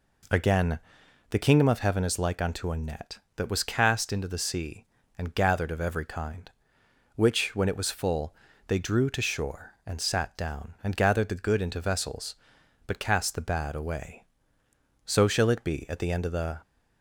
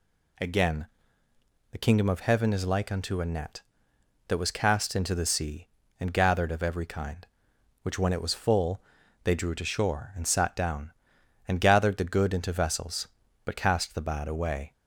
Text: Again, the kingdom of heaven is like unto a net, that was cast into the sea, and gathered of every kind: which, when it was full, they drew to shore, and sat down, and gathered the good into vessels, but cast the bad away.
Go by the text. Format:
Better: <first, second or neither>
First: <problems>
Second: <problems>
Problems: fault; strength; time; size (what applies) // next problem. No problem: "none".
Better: second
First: goes on to say "So shall it be at the end of the"; from 15.0 s on; 1.5 s long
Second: none